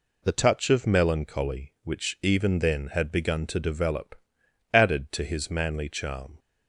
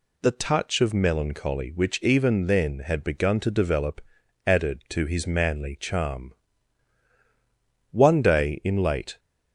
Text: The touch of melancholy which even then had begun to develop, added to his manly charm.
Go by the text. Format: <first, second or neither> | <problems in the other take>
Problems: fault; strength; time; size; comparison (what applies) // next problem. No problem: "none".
first | goes on to say "One day in late"; noticeable; from 7.9 s on; 1.2 s long